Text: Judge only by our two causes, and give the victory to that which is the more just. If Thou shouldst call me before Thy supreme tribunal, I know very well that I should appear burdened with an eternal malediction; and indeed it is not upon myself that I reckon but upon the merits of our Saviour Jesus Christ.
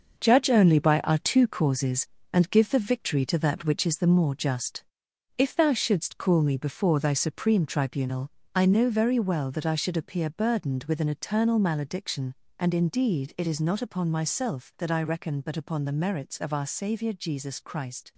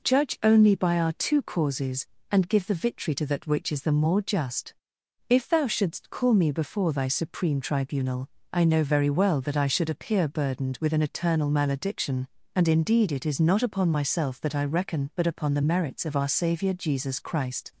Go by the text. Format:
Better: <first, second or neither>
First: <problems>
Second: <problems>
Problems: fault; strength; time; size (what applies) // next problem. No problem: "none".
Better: second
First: gets quieter; strong; throughout; 8 dB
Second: none